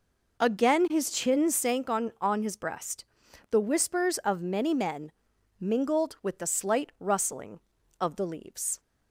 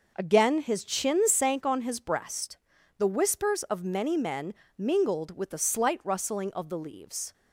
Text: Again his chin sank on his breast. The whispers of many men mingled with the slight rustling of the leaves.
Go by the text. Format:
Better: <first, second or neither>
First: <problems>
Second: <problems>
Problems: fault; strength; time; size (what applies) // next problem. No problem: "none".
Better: second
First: says "on" twice; at 2.2 s // pauses between "men" and "mingled"; noticeable; at 5.0 s; 0.50 s long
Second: pauses between "men" and "mingled"; slight; at 4.5 s; 0.24 s long